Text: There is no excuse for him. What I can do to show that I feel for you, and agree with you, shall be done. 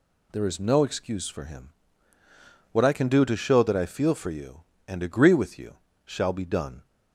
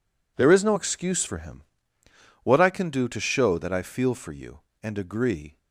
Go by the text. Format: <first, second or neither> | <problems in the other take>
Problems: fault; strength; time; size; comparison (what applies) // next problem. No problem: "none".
first | stops before "with you shall be done"; at 5.5 s